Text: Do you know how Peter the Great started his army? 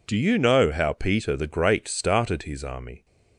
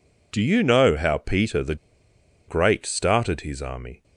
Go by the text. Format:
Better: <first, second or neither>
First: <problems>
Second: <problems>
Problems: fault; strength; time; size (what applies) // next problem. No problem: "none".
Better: first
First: none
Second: pauses between "the" and "Great"; noticeable; at 1.7 s; 0.72 s long